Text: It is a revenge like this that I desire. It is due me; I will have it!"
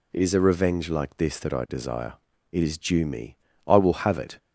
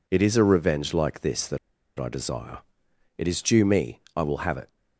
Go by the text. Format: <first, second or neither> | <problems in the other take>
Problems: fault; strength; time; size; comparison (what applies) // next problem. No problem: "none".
first | pauses between "that" and "I"; at 1.5 s; 0.39 s long